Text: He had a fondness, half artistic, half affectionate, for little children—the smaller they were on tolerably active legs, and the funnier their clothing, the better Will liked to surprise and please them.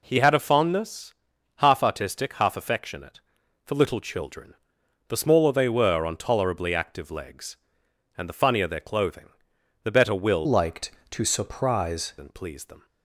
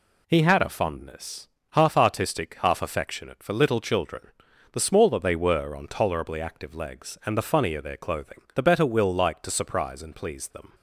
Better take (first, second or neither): second